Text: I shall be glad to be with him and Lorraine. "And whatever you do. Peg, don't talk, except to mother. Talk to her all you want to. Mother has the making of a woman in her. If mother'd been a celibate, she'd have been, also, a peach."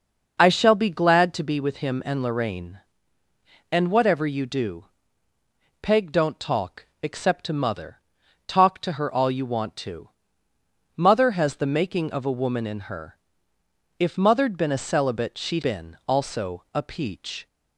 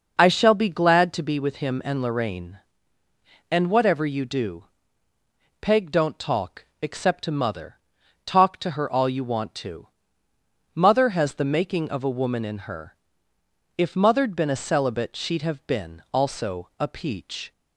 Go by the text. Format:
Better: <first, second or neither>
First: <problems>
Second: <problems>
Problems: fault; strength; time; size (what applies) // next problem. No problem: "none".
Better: second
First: skips "have"; at 15.6 s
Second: none